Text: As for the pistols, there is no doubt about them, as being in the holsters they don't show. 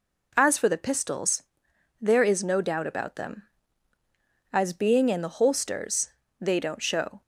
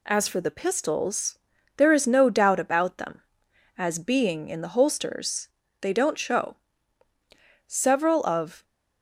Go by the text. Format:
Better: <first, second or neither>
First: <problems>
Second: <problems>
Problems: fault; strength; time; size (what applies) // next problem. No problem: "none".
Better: first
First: pauses between "holsters" and "they"; slight; at 6.0 s; 0.30 s long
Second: pauses between "holsters" and "they"; slight; at 5.4 s; 0.34 s long // goes on to say "Several of"; noticeable; from 7.6 s on; 0.98 s long